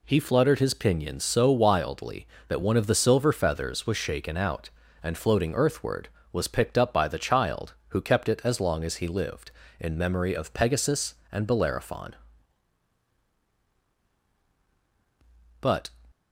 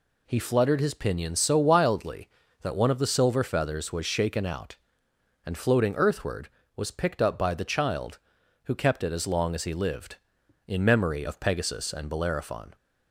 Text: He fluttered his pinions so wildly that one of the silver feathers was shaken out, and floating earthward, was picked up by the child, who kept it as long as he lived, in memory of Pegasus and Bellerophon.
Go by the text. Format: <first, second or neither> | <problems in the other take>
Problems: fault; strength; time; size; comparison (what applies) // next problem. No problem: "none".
second | goes on to say "But"; slight; from 15.6 s on; 0.30 s long